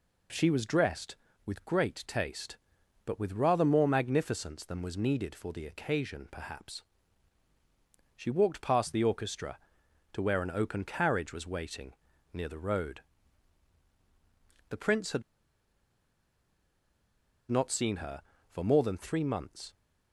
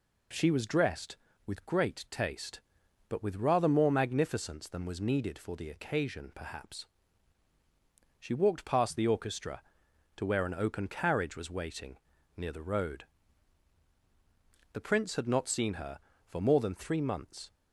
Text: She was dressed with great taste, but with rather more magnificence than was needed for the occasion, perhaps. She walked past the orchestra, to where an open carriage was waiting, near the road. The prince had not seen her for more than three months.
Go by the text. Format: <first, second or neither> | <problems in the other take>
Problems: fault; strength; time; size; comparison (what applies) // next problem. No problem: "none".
second | pauses between "had" and "not"; strong; at 15.2 s; 2.2 s long